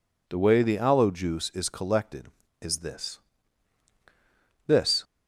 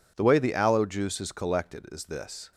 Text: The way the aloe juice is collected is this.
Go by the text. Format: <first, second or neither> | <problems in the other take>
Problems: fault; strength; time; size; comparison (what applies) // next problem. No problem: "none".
second | says "this" twice; at 4.6 s